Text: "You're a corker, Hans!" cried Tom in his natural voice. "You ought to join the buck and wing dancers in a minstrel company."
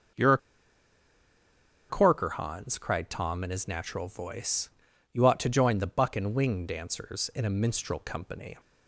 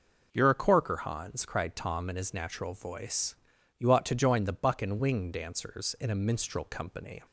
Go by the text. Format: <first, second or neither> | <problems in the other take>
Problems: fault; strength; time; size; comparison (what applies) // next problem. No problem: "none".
second | pauses between "a" and "corker"; strong; at 0.3 s; 1.5 s long